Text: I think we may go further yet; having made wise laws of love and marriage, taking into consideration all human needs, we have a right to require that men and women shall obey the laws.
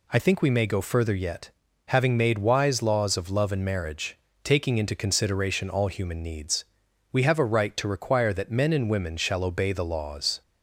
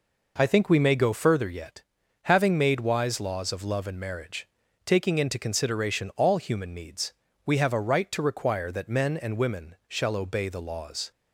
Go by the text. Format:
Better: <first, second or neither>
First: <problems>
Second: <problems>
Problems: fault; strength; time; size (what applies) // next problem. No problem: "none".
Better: neither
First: none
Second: none